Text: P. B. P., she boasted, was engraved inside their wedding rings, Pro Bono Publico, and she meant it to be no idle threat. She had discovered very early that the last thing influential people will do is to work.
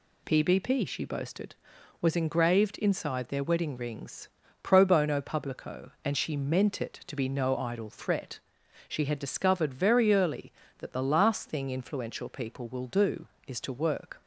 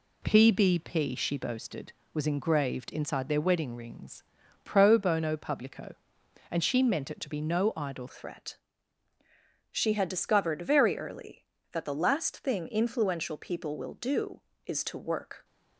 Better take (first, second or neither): first